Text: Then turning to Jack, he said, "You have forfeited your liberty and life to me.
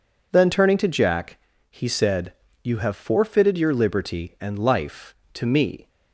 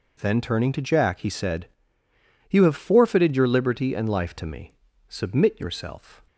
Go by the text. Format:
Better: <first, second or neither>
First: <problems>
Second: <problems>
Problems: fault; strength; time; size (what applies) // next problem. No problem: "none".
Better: first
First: none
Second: goes on to say "Submit yourself"; noticeable; from 5.0 s on; 1.1 s long